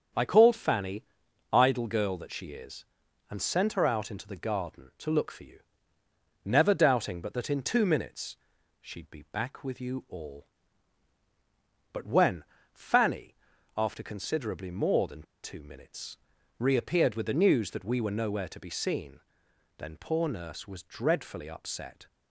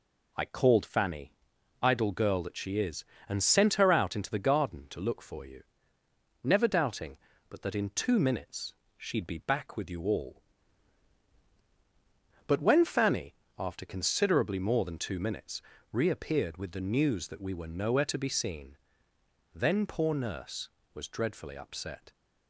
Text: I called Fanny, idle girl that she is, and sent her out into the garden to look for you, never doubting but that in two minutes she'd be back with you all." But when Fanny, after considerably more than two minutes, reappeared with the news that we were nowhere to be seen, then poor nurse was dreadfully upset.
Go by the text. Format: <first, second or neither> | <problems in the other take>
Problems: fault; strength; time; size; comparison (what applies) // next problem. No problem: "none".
second | starts louder than the rest; strong; until 1.6 s; 7.5 dB // pauses between "minutes" and "she'd"; at 8.3 s; 0.44 s long; slight in the second // pauses between "when" and "Fanny"; slight; at 12.4 s; 0.30 s long // pauses between "than" and "two"; slight; at 15.2 s; 0.20 s long